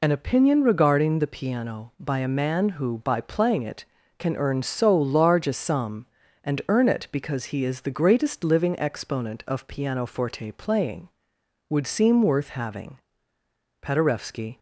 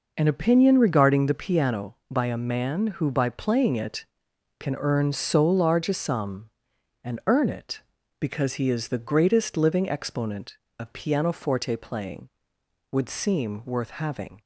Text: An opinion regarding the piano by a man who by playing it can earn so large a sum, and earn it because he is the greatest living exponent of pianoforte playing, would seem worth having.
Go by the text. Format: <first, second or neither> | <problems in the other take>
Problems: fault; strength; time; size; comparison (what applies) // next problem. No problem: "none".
second | goes on to say "Paderewski"; noticeable; from 13.8 s on; 0.76 s long